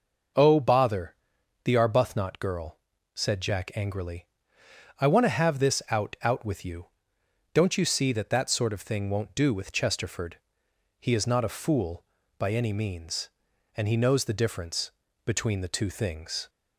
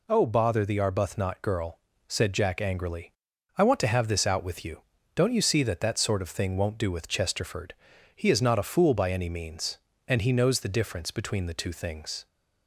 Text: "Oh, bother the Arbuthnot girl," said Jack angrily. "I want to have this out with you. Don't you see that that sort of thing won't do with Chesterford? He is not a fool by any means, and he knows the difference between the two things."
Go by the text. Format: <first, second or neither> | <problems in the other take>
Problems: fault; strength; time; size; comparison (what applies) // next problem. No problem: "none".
second | pauses between "bother" and "the"; noticeable; at 1.1 s; 0.50 s long // says "out" twice; at 6.2 s // pauses between "difference" and "between"; slight; at 14.9 s; 0.34 s long